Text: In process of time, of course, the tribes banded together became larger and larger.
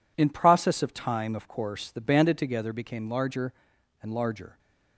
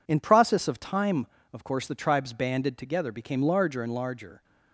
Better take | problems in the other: second | skips "tribes"; at 2.0 s

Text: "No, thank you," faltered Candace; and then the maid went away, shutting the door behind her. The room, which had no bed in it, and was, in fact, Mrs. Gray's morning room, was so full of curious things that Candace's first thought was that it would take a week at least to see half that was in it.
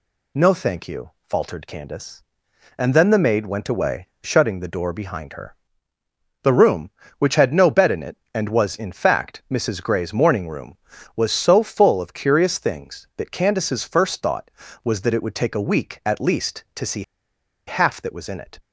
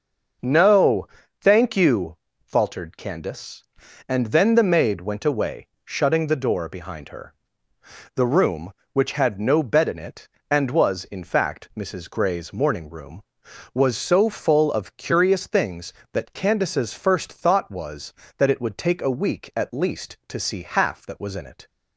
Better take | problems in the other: second | pauses between "see" and "half"; noticeable; at 17.0 s; 0.65 s long

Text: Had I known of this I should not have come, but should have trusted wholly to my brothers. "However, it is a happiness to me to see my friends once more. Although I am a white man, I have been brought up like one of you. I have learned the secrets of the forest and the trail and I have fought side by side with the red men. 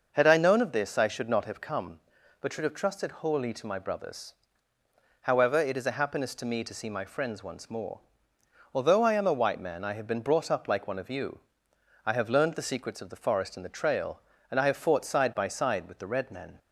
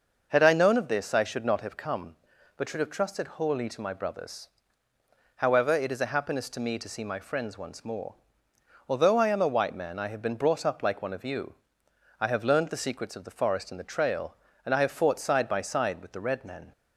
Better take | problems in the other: neither | starts louder than the rest; noticeable; the same in both

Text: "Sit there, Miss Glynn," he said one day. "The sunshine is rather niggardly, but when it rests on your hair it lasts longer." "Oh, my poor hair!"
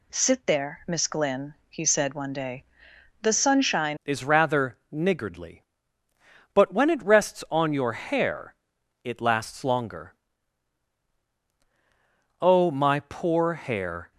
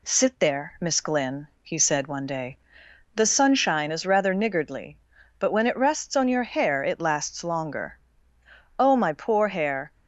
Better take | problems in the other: second | changes voice at "is"; from 4.0 s on; 10.1 s long // pauses between "hair" and "it"; noticeable; at 8.5 s; 0.50 s long

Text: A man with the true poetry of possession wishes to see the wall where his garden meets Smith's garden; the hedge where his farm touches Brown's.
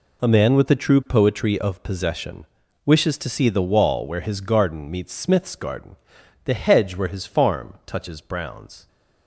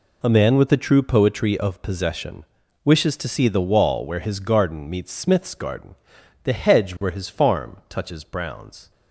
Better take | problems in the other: neither | pauses between "possession" and "wishes"; the same in both

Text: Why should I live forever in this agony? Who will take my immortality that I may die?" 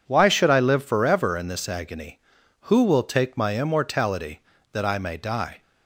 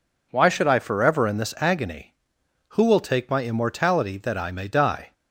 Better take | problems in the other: first | skips "live"; at 0.7 s

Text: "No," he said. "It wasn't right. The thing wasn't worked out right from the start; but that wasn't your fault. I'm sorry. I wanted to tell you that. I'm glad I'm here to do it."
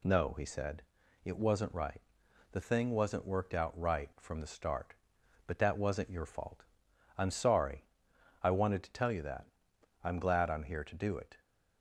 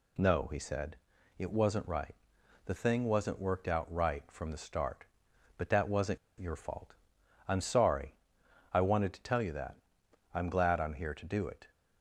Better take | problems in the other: first | pauses between "wasn't" and "your"; slight; at 6.1 s; 0.22 s long

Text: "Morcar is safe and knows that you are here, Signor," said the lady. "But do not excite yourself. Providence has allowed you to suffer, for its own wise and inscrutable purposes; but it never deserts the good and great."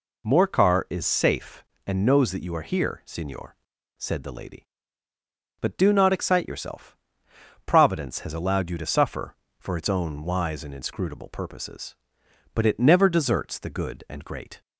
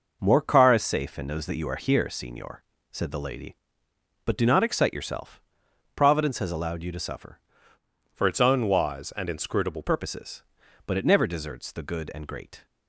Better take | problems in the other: first | changes voice from "for" to "inscrutable"; from 8.1 to 9.8 s; 1.7 s long

